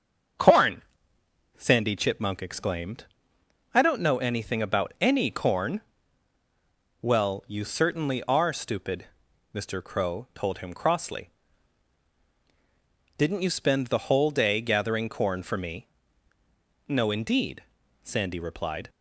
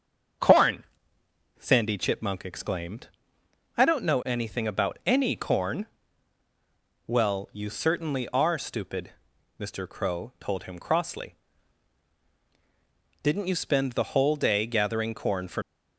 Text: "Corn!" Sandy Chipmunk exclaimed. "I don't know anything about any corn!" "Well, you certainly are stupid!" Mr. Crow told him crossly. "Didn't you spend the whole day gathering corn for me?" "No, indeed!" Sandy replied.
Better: first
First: starts louder than the rest; strong; until 2.1 s; 7.5 dB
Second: starts louder than the rest; strong; until 2.1 s; 7.5 dB // stops before "me No indeed Sandy replied"; at 15.6 s

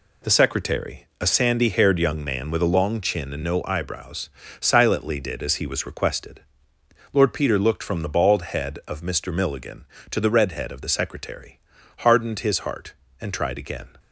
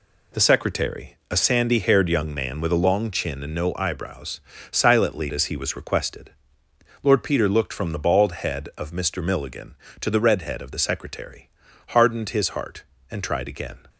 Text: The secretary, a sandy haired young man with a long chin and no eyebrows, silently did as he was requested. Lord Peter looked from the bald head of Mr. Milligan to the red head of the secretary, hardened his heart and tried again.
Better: first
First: none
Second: skips "did"; at 5.3 s

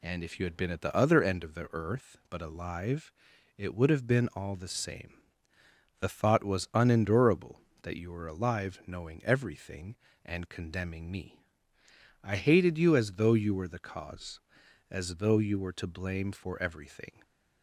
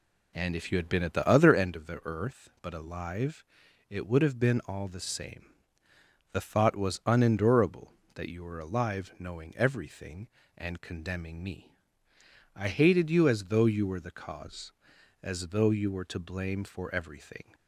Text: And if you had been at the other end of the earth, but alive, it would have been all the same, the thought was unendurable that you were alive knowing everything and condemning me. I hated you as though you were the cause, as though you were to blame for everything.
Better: first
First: none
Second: starts louder than the rest; slight; until 1.7 s; 3 dB

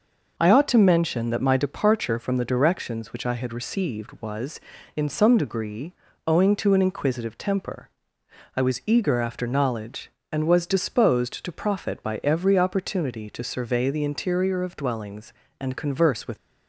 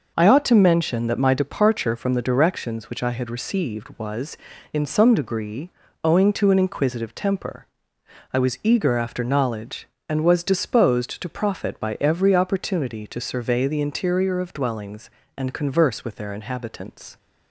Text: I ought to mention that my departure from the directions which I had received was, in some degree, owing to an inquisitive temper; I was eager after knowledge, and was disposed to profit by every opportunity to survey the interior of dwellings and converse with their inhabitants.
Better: second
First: stops before "their inhabitants"; at 16.3 s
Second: none

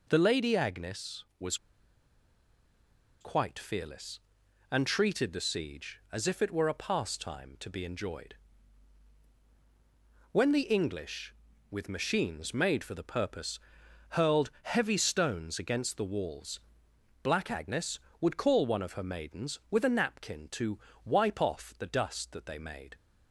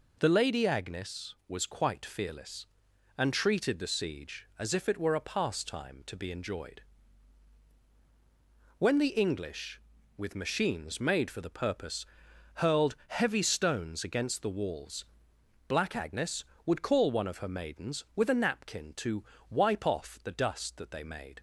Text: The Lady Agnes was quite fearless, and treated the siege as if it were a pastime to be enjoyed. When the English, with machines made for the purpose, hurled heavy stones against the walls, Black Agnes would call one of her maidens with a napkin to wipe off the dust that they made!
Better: second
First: pauses between "was" and "quite"; strong; at 1.5 s; 1.6 s long // pauses between "to" and "wipe"; slight; at 20.7 s; 0.26 s long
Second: pauses between "to" and "wipe"; slight; at 19.2 s; 0.26 s long

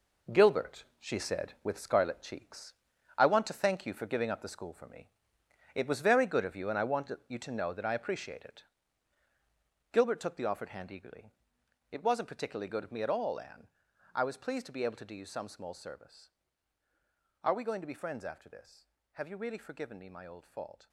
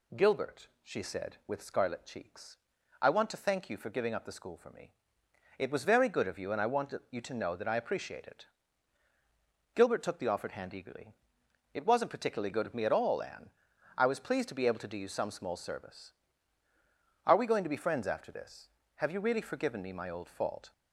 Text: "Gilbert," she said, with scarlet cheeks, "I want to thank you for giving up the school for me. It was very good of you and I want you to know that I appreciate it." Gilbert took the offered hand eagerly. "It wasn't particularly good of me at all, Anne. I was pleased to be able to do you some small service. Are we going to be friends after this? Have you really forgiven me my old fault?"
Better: second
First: gets quieter; strong; throughout; 9.5 dB // pauses between "want" and "you"; slight; at 7.1 s; 0.16 s long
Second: pauses between "want" and "you"; slight; at 6.9 s; 0.16 s long

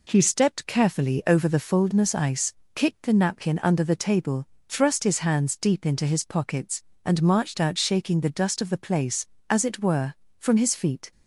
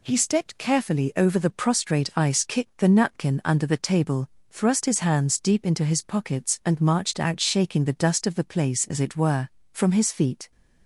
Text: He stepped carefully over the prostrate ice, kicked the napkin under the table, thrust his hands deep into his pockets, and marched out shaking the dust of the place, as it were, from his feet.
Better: second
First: says "foldness" for "prostrate"; at 1.5 s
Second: none

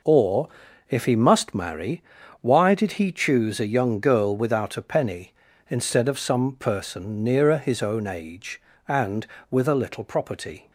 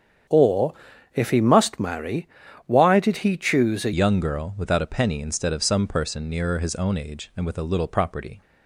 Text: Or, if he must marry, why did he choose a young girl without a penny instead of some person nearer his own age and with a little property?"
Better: first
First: none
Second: starts louder than the rest; strong; until 1.7 s; 8.5 dB // changes voice at "young"; from 3.9 s on; 4.5 s long

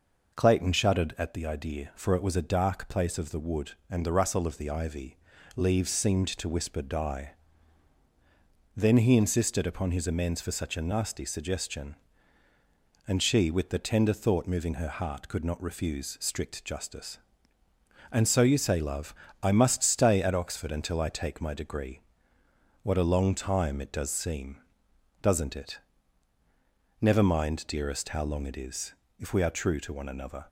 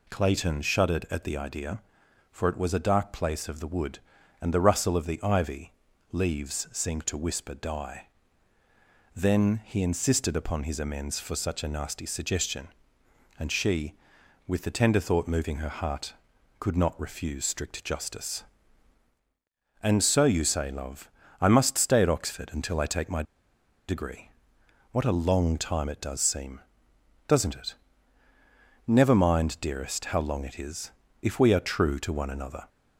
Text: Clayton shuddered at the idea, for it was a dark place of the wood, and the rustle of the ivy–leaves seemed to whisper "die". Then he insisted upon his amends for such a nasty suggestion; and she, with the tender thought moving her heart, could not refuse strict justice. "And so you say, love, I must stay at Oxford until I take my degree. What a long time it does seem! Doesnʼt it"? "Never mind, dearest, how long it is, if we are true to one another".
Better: first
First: none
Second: pauses between "my" and "degree"; noticeable; at 23.2 s; 0.65 s long

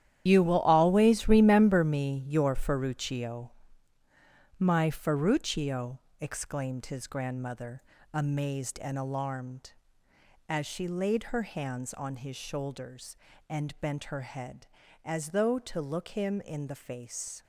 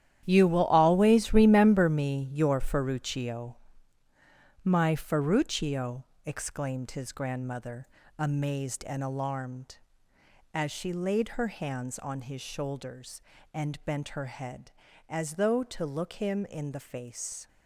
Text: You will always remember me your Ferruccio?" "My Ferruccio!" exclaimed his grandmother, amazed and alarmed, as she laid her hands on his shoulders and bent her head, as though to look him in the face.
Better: second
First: loses the start of "You"; at 0.2 s; 70 ms // starts louder than the rest; strong; until 1.2 s; 10.5 dB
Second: starts louder than the rest; strong; until 1.2 s; 11 dB

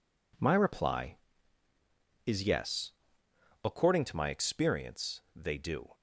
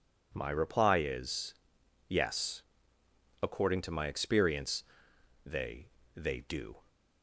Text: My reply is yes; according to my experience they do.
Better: first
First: pauses between "experience" and "they"; slight; at 5.2 s; 0.16 s long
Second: pauses between "is" and "yes"; noticeable; at 1.5 s; 0.56 s long // pauses between "experience" and "they"; noticeable; at 4.8 s; 0.62 s long // says "they" twice; at 6.1 s

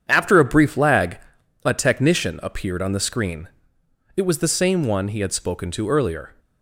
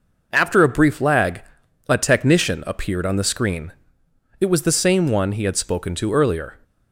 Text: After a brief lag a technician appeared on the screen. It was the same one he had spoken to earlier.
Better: second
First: starts louder than the rest; strong; until 1.5 s; 8 dB // pauses between "lag" and "a"; noticeable; at 1.1 s; 0.46 s long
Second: pauses between "lag" and "a"; noticeable; at 1.4 s; 0.46 s long

